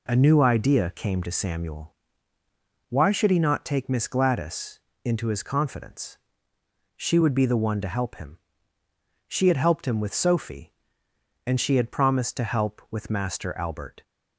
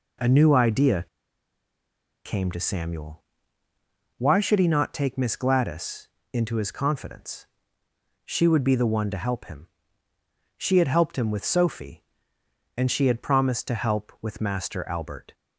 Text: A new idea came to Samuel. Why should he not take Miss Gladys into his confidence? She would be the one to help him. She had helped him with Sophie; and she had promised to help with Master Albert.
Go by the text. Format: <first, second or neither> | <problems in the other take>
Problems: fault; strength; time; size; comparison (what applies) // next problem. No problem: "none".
first | pauses between "idea" and "came"; at 1.0 s; 1.1 s long // pauses between "Gladys" and "into"; slight; at 6.0 s; 0.24 s long; slight in the first